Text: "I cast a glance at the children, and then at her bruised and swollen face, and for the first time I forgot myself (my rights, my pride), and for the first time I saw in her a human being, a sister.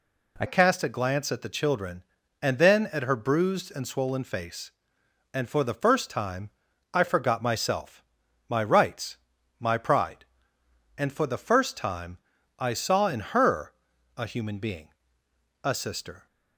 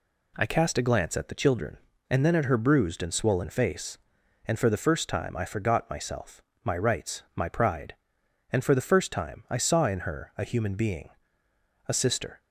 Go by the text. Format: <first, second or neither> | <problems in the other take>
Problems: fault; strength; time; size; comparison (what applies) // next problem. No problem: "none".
second | changes voice at "cast"; from 0.4 s on; 15.8 s long // pauses between "time" and "I"; at 6.4 s; 0.42 s long // pauses between "time" and "I"; at 12.1 s; 0.40 s long // pauses between "her" and "a"; noticeable; at 13.7 s; 0.46 s long